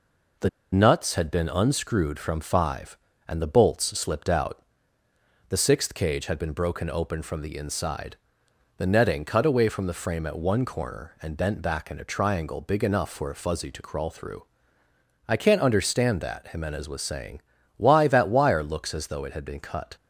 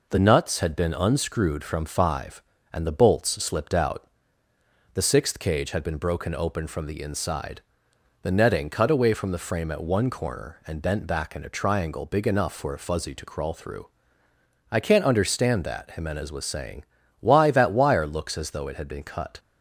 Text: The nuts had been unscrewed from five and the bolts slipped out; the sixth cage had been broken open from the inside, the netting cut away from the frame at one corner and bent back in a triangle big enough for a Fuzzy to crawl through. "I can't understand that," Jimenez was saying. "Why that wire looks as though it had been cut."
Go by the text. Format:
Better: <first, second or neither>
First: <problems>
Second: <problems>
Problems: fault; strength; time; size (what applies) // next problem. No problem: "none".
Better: second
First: pauses between "The" and "nuts"; slight; at 0.4 s; 0.23 s long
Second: none